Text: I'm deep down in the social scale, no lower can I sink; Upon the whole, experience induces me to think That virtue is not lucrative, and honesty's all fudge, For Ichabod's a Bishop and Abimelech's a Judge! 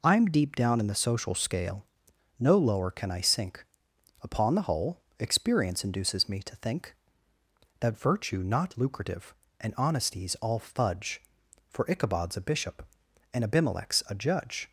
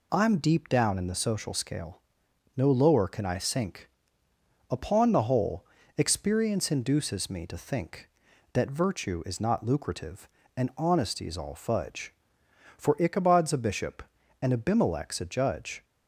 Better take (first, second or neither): second